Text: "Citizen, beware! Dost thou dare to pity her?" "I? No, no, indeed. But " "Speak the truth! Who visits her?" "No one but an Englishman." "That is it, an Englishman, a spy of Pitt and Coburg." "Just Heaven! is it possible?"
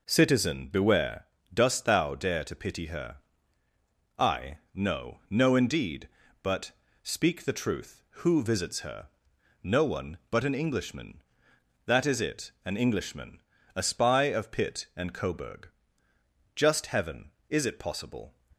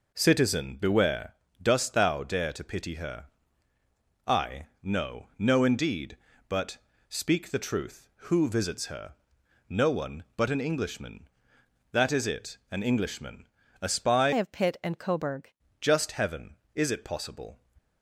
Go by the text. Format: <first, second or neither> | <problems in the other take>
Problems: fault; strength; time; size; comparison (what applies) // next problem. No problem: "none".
first | changes voice from "of" to "Coburg"; from 14.3 to 15.5 s; 1.2 s long